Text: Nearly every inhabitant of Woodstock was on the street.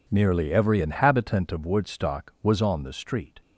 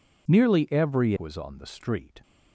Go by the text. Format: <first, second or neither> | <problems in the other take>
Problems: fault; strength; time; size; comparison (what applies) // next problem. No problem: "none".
first | skips "inhabitant of Woodstock"; at 1.1 s